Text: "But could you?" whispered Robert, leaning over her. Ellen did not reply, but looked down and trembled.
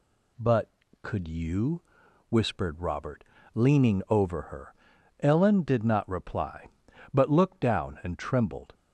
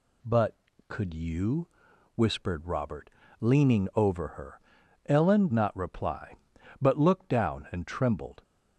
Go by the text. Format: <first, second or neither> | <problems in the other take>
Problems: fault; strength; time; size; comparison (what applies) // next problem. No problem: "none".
first | skips "did"; at 5.5 s